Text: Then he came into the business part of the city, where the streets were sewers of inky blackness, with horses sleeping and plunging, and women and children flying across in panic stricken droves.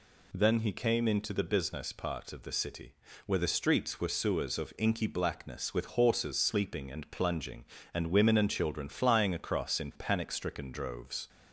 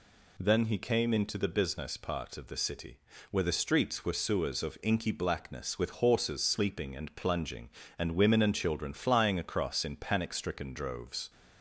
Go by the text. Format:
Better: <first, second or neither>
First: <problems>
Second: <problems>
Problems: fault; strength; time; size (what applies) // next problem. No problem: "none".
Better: neither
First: none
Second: none